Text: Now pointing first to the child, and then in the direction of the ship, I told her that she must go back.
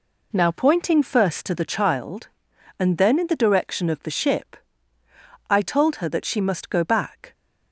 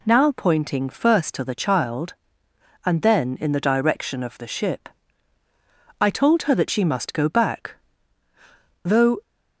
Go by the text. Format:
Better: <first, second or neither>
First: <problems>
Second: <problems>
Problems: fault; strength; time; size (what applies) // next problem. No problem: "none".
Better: first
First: none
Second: goes on to say "Though"; slight; from 8.8 s on; 0.40 s long